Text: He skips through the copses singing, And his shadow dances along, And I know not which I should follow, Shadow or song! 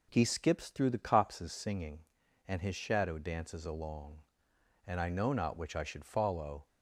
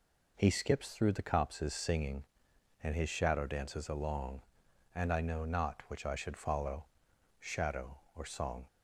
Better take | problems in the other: second | stops before "Shadow or song"; at 6.6 s

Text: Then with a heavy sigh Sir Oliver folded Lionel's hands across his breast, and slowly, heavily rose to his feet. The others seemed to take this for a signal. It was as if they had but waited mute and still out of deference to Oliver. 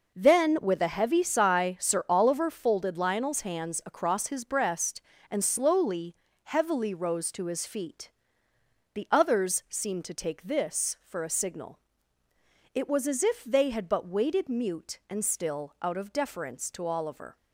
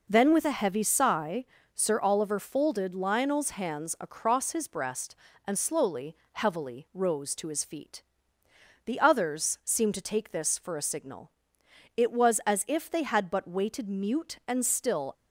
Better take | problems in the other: first | pauses between "sigh" and "Sir"; slight; at 1.4 s; 0.32 s long // stops before "out of deference to Oliver"; at 15.1 s

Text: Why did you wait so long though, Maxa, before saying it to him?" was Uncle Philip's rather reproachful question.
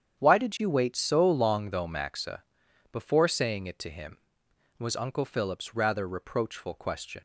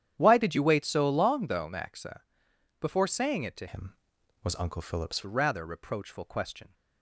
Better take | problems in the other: first | starts louder than the rest; strong; until 1.1 s; 10 dB; strong in the first // changes voice from "him" to "Philip's"; from 3.6 to 5.2 s; 1.6 s long

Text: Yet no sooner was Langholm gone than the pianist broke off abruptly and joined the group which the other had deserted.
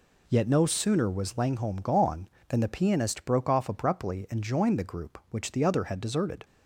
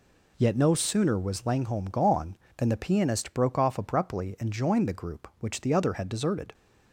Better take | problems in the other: neither | none

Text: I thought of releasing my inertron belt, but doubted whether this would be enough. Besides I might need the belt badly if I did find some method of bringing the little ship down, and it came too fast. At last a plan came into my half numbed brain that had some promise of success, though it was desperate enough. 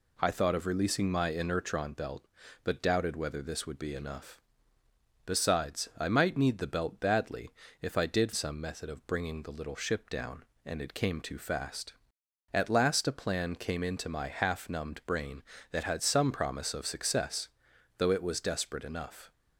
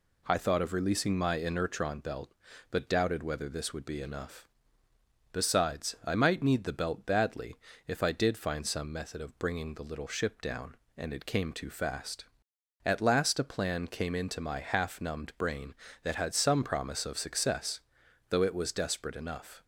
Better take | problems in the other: second | pauses between "badly" and "if"; slight; at 7.4 s; 0.32 s long; slight in the second // skips "find"; at 8.3 s

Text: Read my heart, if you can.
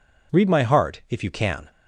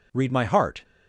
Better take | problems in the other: first | stops before "if you can"; at 0.8 s

